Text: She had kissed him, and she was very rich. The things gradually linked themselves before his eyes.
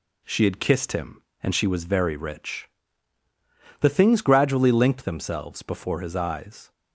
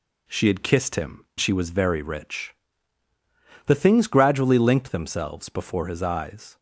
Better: first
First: none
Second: skips "and"; at 1.3 s

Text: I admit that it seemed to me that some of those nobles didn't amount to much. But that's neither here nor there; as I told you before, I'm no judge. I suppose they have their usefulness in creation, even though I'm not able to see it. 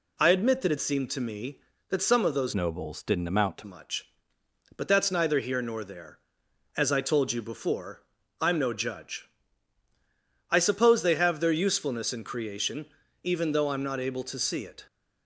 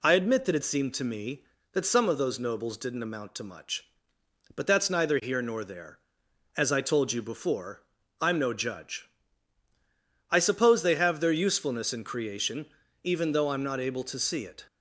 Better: second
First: changes voice from "nobles" to "to"; from 2.5 to 3.6 s; 1.1 s long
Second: none

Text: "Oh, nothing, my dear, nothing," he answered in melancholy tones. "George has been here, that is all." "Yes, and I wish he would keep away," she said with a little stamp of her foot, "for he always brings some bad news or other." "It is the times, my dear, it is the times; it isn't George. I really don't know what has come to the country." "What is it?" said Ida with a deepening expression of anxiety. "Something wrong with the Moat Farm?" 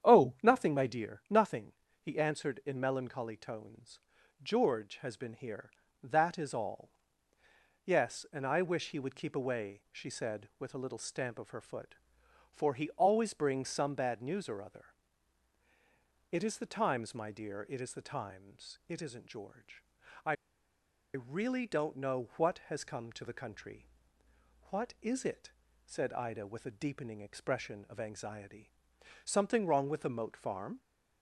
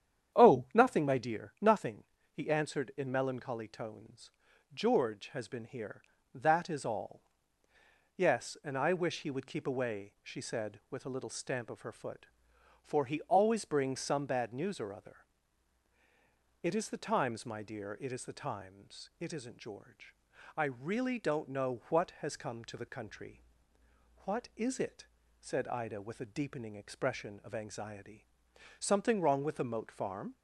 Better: second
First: starts louder than the rest; strong; until 1.1 s; 9 dB // pauses between "I" and "really"; noticeable; at 20.3 s; 0.80 s long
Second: starts louder than the rest; strong; until 1.4 s; 9 dB

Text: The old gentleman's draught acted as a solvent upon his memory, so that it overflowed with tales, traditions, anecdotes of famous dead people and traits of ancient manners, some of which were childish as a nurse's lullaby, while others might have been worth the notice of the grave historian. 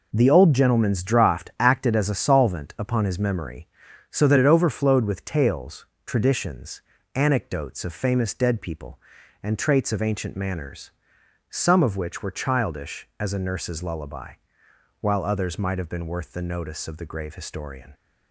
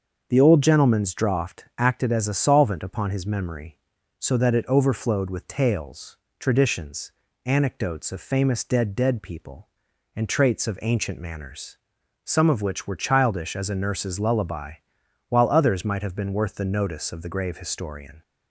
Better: first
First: none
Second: starts louder than the rest; until 1.3 s; 6.5 dB // says "dead" twice; at 8.9 s

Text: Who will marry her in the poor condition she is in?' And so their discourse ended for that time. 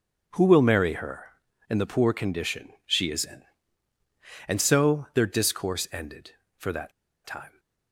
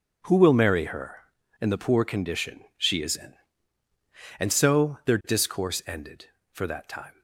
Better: second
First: pauses between "that" and "time"; slight; at 6.9 s; 0.35 s long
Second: none

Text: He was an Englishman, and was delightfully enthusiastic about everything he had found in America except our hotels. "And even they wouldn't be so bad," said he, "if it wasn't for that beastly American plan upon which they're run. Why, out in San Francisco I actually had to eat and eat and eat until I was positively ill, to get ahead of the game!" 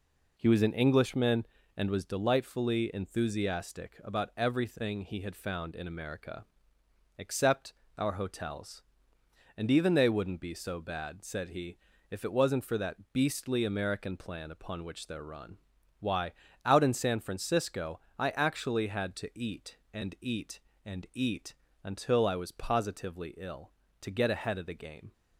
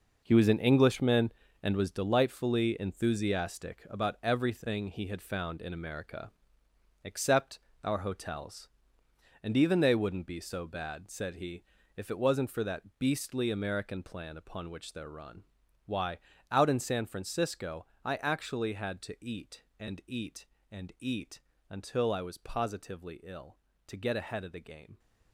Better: first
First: pauses between "America" and "except"; noticeable; at 6.4 s; 0.74 s long // pauses between "except" and "our"; slight; at 7.7 s; 0.24 s long // pauses between "Francisco" and "I"; slight; at 17.9 s; 0.20 s long // pauses between "eat" and "until"; slight; at 21.5 s; 0.28 s long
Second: gets quieter; strong; throughout; 10 dB // pauses between "America" and "except"; noticeable; at 6.3 s; 0.74 s long // pauses between "except" and "our"; slight; at 7.5 s; 0.24 s long // pauses between "Francisco" and "I"; slight; at 17.8 s; 0.20 s long // pauses between "eat" and "until"; slight; at 21.4 s; 0.28 s long

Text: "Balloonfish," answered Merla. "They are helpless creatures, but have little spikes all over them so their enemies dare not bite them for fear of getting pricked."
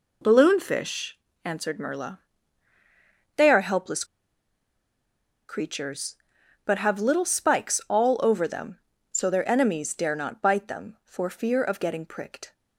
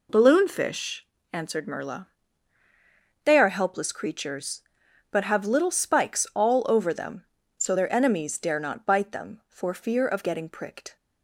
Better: second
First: pauses between "helpless" and "creatures"; strong; at 4.0 s; 1.4 s long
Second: none

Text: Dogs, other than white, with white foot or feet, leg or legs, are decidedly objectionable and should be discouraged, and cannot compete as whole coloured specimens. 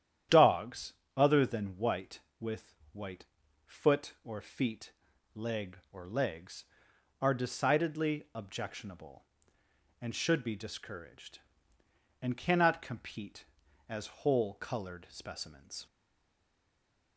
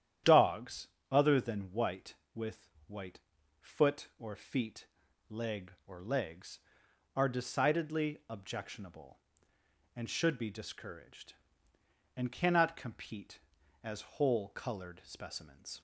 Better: second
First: starts louder than the rest; strong; until 1.5 s; 10.5 dB // pauses between "with" and "white"; slight; at 2.7 s; 0.16 s long // pauses between "white" and "foot"; at 3.2 s; 0.42 s long // stays silent after the last word; noticeable; from 15.8 s on; 1.3 s long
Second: starts louder than the rest; strong; until 1.4 s; 10.5 dB // pauses between "with" and "white"; slight; at 2.7 s; 0.16 s long // pauses between "white" and "foot"; at 3.1 s; 0.42 s long

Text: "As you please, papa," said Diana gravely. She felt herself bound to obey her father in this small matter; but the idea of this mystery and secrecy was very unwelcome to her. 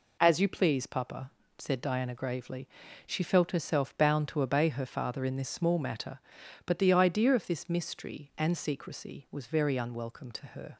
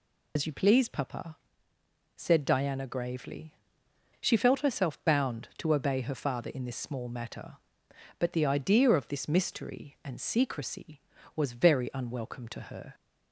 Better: first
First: none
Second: loses the start of "As"; at 0.3 s; 100 ms

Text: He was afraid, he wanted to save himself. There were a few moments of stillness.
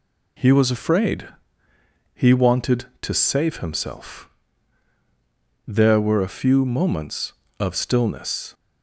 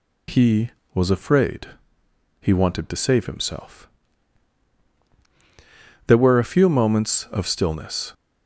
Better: neither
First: none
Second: none

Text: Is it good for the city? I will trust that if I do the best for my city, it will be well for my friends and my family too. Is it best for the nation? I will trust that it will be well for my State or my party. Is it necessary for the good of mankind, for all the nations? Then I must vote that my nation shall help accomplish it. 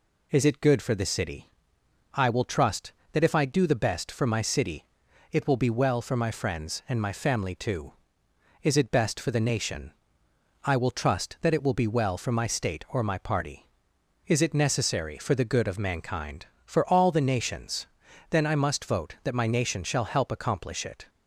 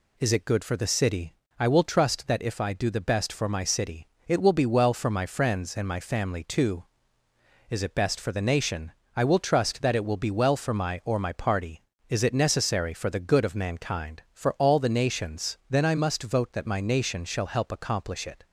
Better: first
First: none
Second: skips "State"; at 11.0 s

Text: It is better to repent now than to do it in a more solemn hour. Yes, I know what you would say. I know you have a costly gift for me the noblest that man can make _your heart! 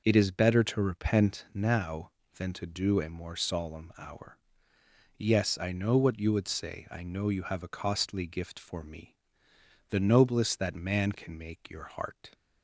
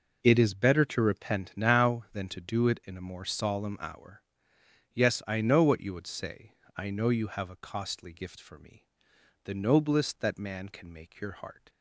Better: second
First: skips "it in"; at 3.0 s // pauses between "me" and "the"; noticeable; at 9.1 s; 0.76 s long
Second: pauses between "me" and "the"; noticeable; at 8.8 s; 0.60 s long

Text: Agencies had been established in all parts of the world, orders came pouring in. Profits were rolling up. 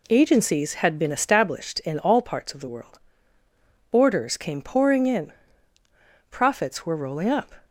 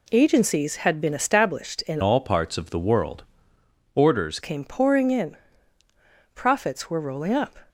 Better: first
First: none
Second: changes voice from "all" to "orders"; from 2.0 to 4.3 s; 2.3 s long

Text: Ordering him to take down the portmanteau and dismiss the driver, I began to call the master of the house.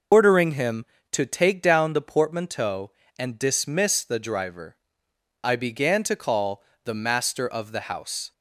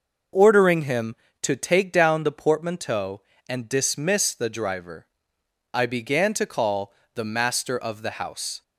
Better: second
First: loses the start of "Ordering"; at 0.1 s; 90 ms // pauses between "call" and "the"; slight; at 6.6 s; 0.22 s long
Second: pauses between "call" and "the"; slight; at 6.9 s; 0.22 s long

